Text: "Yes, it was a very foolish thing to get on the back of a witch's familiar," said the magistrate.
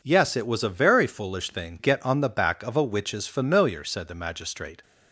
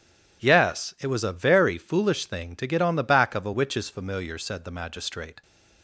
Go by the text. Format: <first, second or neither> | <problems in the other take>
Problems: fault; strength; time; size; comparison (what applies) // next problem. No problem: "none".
second | skips "to"; at 1.7 s